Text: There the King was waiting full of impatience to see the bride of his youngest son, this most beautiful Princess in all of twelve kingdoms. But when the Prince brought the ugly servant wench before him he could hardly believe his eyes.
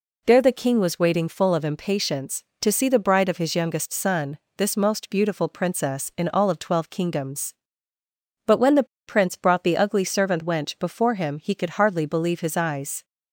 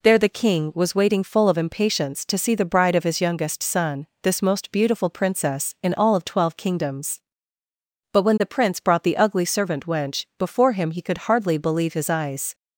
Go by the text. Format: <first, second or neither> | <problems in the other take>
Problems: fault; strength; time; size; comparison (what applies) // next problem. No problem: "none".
second | pauses between "the" and "Prince"; slight; at 8.8 s; 0.22 s long